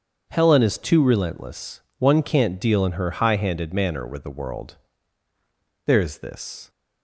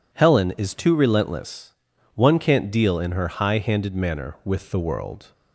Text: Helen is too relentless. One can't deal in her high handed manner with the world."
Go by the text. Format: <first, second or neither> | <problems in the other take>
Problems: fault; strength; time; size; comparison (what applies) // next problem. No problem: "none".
second | starts louder than the rest; until 1.3 s; 7 dB // goes on to say "There's this"; noticeable; from 5.8 s on; 0.84 s long